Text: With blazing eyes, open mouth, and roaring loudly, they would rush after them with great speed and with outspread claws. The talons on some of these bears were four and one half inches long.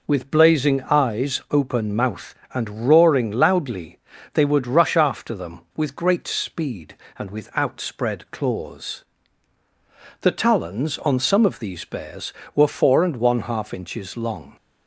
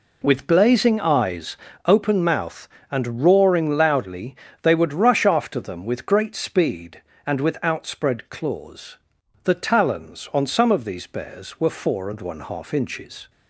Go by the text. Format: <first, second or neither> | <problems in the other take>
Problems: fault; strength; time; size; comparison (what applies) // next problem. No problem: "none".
first | stops before "long"; at 13.2 s